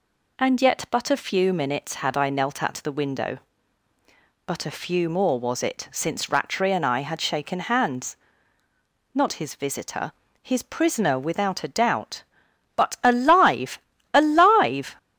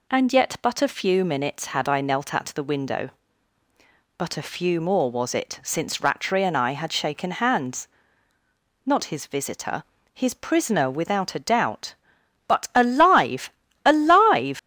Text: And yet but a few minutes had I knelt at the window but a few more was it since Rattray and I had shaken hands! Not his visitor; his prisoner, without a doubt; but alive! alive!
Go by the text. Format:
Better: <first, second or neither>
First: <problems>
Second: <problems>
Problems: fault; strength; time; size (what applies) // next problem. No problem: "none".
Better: first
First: none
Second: leaves "alive" unfinished; at 14.5 s; 95 ms